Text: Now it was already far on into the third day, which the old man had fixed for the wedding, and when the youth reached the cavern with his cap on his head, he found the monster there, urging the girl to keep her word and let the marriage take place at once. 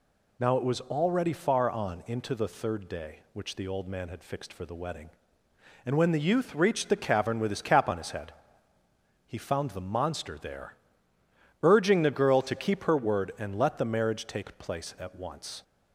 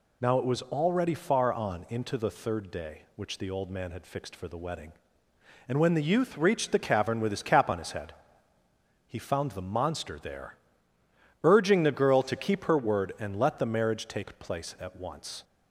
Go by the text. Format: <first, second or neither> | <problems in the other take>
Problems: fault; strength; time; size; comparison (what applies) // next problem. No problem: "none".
neither | none